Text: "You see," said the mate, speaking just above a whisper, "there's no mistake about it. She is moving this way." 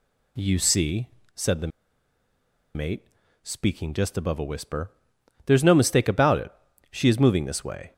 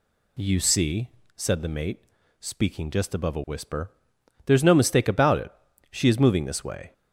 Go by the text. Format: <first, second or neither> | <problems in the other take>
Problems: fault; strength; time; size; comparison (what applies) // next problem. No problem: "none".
second | pauses between "the" and "mate"; at 1.7 s; 1.0 s long